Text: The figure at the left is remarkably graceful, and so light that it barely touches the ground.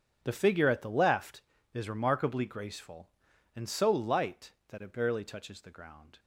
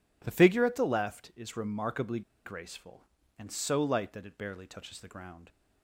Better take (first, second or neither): first